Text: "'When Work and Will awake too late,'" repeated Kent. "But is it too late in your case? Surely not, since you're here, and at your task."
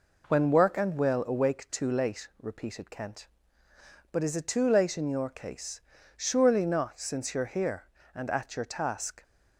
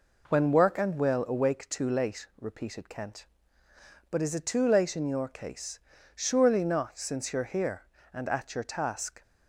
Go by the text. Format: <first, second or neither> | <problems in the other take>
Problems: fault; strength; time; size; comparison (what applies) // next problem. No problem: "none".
neither | none